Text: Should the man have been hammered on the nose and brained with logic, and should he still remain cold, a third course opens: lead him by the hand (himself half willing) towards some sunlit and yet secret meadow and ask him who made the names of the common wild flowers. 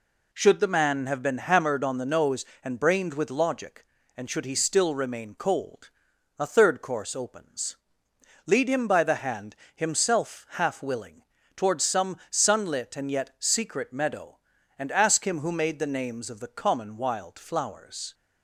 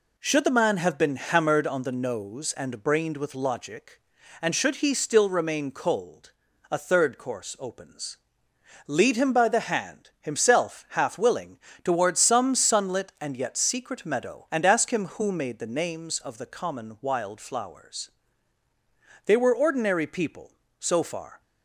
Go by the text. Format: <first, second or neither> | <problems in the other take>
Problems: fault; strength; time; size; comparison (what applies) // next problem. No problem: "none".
first | goes on to say "They were ordinary people so far"; strong; from 19.2 s on; 2.1 s long